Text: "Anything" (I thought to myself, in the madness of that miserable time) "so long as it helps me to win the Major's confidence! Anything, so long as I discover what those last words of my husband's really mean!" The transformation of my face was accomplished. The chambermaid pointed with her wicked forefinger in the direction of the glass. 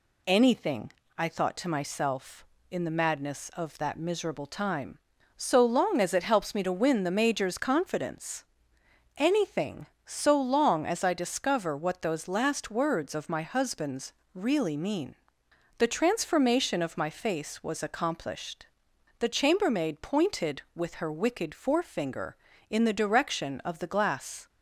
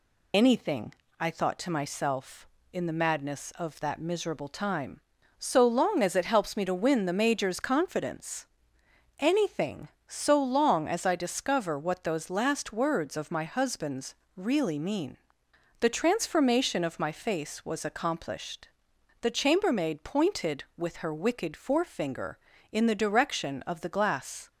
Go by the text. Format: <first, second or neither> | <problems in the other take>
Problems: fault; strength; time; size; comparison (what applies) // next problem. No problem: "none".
first | loses the start of "Anything"; at 0.3 s; 55 ms // pauses between "husband's" and "really"; slight; at 14.1 s; 0.22 s long; slight in the first